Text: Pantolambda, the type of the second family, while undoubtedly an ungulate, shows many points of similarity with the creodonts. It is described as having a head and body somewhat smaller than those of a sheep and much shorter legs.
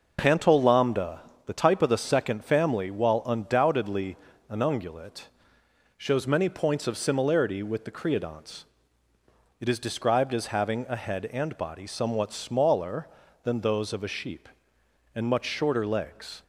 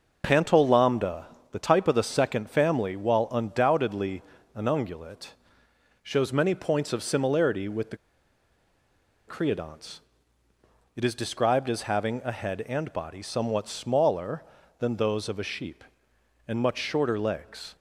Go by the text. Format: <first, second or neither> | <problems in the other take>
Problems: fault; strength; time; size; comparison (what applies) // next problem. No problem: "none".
first | pauses between "undoubtedly" and "an"; slight; at 4.2 s; 0.32 s long; slight in the first // pauses between "the" and "creodonts"; strong; at 7.9 s; 1.3 s long